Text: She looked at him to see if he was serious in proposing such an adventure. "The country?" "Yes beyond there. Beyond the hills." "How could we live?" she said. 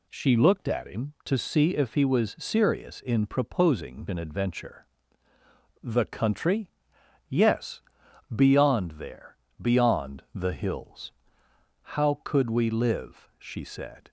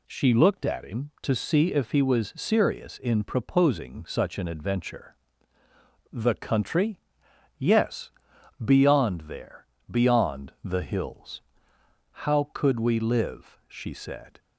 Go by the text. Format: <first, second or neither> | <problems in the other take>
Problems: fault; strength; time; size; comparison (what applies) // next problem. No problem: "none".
second | skips "such"; at 4.0 s // pauses between "Yes" and "beyond"; noticeable; at 7.8 s; 0.52 s long; noticeable in the second